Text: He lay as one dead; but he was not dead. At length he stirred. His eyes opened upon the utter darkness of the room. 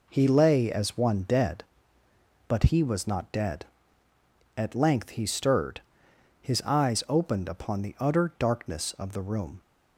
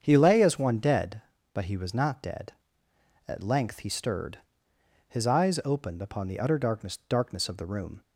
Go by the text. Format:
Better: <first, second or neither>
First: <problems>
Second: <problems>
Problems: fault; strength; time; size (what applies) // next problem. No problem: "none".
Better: first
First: none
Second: starts louder than the rest; strong; until 1.0 s; 7.5 dB // says "darkness" twice; at 7.0 s